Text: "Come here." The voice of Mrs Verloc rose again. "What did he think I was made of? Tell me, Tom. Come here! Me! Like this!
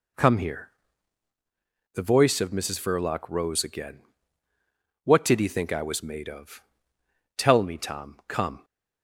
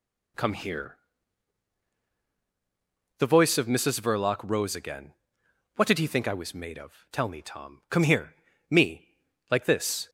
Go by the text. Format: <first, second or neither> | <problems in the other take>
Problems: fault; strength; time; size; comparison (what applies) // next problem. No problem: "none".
second | stops before "here Me Like this"; at 8.6 s